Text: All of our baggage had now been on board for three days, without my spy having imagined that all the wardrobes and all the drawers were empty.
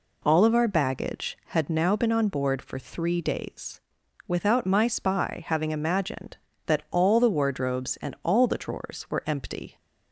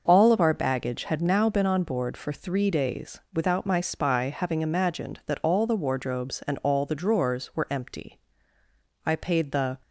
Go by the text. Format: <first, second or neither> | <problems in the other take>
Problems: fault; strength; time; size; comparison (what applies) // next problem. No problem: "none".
first | starts louder than the rest; noticeable; until 1.0 s; 6 dB // goes on to say "I paid the"; noticeable; from 9.0 s on; 0.74 s long